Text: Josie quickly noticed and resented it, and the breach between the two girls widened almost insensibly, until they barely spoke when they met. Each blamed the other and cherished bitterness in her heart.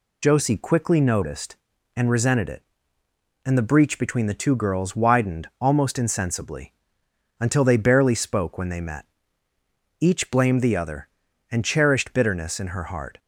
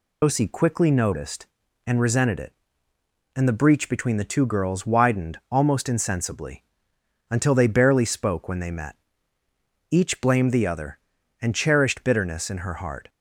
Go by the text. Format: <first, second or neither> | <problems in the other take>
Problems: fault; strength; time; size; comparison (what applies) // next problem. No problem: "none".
first | loses the start of "Josie"; at 0.2 s; 95 ms